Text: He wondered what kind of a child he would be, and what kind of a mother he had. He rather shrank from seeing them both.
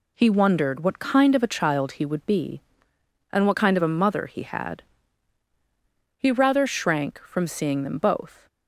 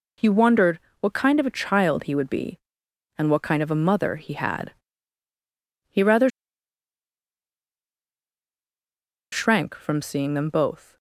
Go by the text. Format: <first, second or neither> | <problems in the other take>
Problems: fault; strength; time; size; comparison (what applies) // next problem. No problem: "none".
first | pauses between "wondered" and "what"; slight; at 0.8 s; 0.18 s long // pauses between "rather" and "shrank"; strong; at 6.2 s; 3.0 s long